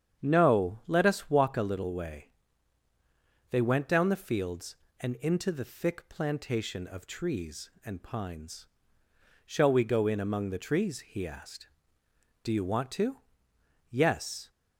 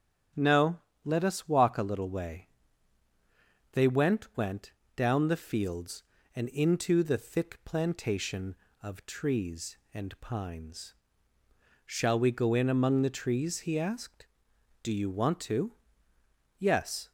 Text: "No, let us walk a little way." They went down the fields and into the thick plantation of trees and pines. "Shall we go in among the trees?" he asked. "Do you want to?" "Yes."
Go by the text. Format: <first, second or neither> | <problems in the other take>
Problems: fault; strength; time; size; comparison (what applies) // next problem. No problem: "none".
first | starts louder than the rest; strong; until 1.6 s; 8.5 dB; strong in the first // says "went" twice; at 4.3 s